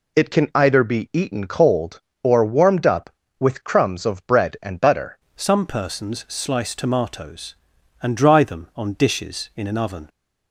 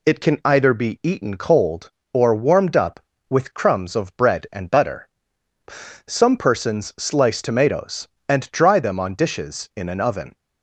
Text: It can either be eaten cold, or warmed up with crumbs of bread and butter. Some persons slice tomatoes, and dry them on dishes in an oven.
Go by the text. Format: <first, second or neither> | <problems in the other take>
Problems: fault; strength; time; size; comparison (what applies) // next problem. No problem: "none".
second | changes voice at "Some"; from 5.3 s on; 4.7 s long